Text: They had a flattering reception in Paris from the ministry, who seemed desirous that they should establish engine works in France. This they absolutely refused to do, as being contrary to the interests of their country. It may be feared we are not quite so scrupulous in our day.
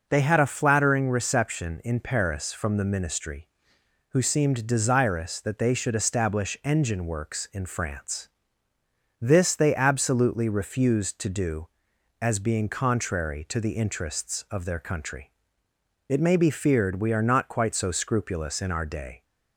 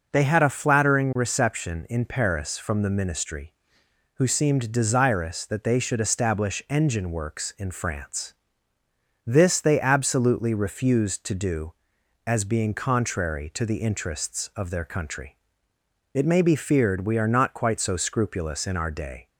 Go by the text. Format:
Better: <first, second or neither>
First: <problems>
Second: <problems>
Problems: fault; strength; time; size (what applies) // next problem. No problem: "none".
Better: neither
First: none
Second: none